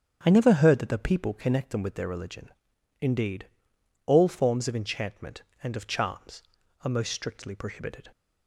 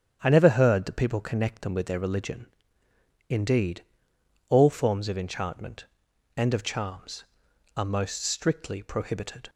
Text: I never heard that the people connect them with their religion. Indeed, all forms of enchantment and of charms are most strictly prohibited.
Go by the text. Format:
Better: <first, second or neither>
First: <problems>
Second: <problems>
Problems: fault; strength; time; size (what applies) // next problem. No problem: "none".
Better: first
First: starts louder than the rest; strong; until 1.2 s; 8 dB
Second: starts louder than the rest; strong; until 1.2 s; 8.5 dB // skips "the"; at 0.9 s